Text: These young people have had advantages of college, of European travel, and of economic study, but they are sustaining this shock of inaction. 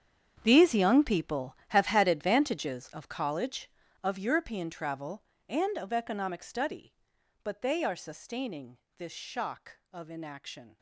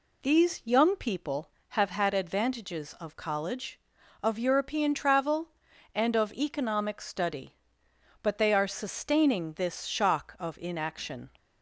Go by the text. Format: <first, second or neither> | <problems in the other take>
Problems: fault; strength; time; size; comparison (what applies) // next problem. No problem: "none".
second | gets quieter; strong; throughout; 16 dB // pauses between "sustaining" and "this"; slight; at 8.7 s; 0.18 s long